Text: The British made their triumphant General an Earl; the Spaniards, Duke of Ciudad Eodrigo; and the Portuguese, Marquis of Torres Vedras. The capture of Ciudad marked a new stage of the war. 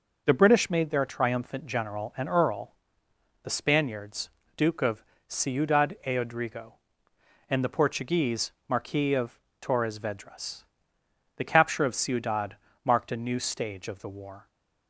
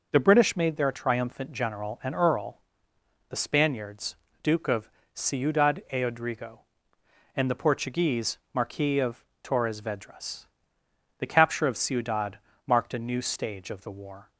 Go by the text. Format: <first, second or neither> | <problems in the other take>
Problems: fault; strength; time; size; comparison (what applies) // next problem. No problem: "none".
neither | pauses between "of" and "Ciudad"; slight; the same in both // pauses between "of" and "Torres"; slight; the same in both // pauses between "Ciudad" and "marked"; slight; the same in both